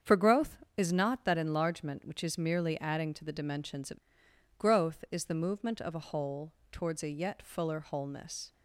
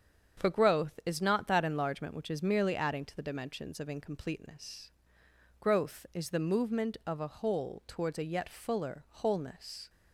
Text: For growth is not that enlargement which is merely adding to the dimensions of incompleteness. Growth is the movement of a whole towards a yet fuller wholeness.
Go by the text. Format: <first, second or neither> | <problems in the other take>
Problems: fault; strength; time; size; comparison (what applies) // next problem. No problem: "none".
second | starts louder than the rest; strong; until 1.2 s; 7.5 dB; strong in the second // skips "incompleteness"; at 4.2 s // pauses between "whole" and "towards"; slight; at 6.5 s; 0.20 s long